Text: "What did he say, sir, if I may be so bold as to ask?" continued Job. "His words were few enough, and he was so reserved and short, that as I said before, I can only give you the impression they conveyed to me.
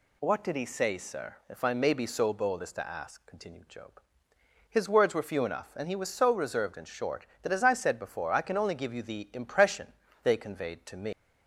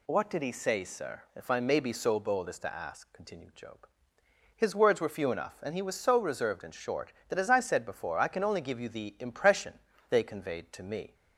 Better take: second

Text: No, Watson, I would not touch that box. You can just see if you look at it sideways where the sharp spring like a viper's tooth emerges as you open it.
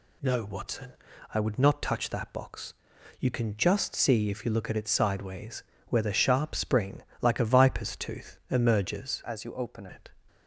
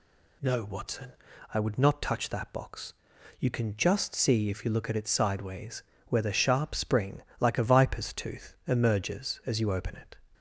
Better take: second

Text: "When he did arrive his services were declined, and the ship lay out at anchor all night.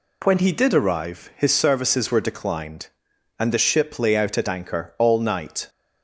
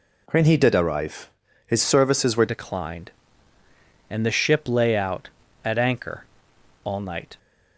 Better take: first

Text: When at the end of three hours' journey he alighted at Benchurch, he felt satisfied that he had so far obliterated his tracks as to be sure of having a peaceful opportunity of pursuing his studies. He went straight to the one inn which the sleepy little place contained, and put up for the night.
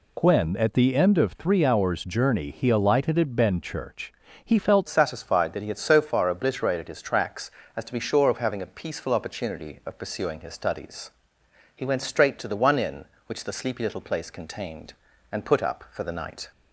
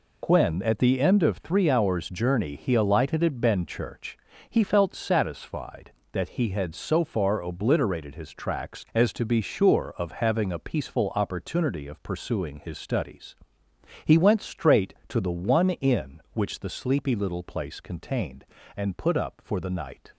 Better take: second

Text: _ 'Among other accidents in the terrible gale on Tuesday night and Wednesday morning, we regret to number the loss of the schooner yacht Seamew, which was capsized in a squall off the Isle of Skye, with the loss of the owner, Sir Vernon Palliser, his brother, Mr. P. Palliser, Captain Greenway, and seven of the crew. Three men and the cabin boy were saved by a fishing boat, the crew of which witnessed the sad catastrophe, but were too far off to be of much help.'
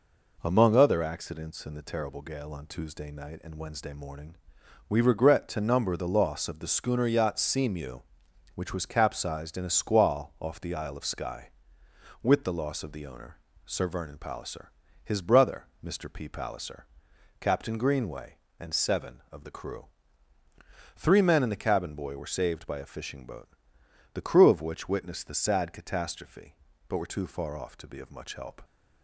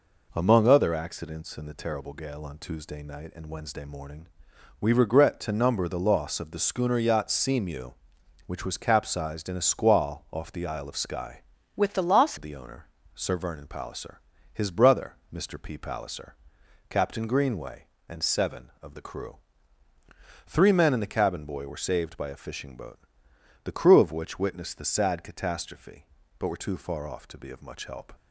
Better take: first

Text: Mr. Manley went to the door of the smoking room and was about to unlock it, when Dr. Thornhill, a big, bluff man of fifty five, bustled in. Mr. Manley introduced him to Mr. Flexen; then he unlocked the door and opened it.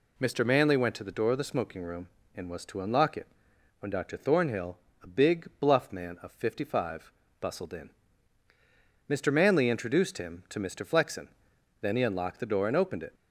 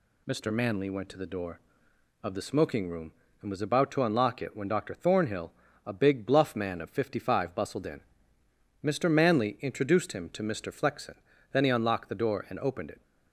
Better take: second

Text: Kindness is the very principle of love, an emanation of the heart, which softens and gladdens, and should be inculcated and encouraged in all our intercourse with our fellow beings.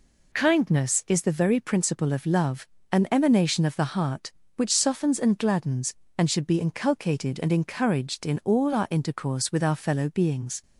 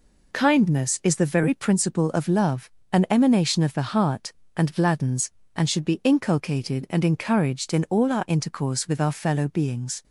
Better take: first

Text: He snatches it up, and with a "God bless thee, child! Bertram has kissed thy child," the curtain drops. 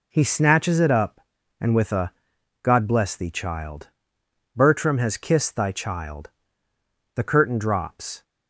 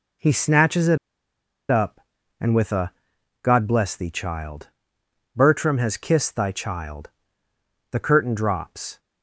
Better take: first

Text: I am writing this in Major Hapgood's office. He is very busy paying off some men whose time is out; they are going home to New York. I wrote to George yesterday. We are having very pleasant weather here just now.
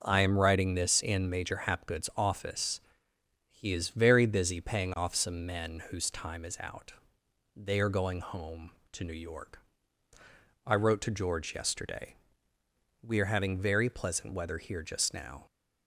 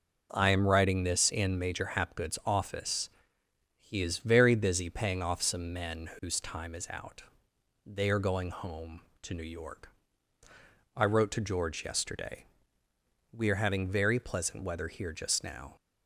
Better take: neither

